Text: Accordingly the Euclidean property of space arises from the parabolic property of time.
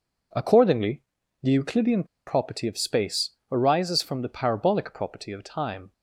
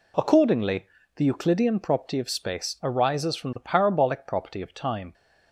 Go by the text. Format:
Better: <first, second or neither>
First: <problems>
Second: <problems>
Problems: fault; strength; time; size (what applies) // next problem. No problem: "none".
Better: second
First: pauses between "Accordingly" and "the"; at 1.0 s; 0.40 s long // pauses between "Euclidean" and "property"; slight; at 2.0 s; 0.22 s long // pauses between "space" and "arises"; slight; at 3.3 s; 0.16 s long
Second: pauses between "Accordingly" and "the"; slight; at 0.8 s; 0.30 s long